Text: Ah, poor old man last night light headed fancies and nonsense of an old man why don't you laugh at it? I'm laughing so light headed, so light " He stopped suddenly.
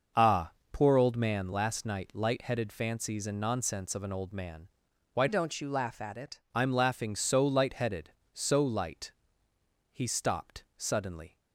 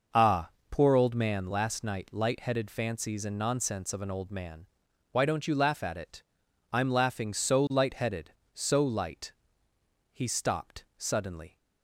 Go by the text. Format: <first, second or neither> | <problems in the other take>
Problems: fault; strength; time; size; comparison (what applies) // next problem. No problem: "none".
second | starts louder than the rest; noticeable; until 1.3 s; 6 dB // pauses between "man" and "why"; noticeable; at 4.6 s; 0.46 s long; noticeable in the second // changes voice from "don't" to "it"; from 5.2 to 6.3 s; 1.1 s long